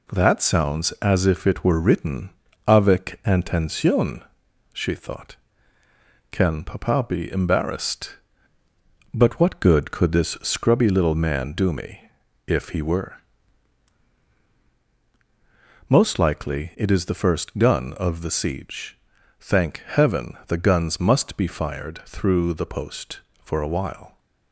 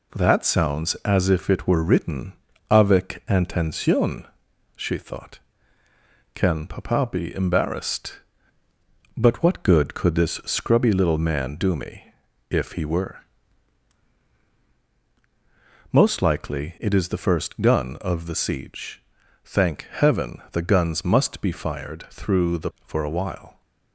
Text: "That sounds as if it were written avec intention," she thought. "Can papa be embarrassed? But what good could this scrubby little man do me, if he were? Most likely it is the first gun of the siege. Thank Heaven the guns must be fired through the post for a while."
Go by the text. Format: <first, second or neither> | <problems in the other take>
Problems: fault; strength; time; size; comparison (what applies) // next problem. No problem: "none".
first | pauses between "written" and "avec"; at 2.3 s; 0.38 s long; also in the first // skips "post"; at 22.7 s